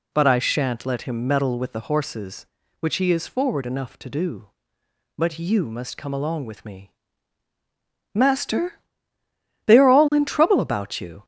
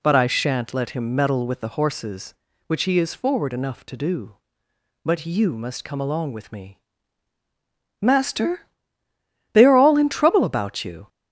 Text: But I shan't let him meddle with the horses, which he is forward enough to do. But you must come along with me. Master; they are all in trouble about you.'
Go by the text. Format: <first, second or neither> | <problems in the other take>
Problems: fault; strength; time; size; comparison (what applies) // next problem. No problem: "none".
neither | none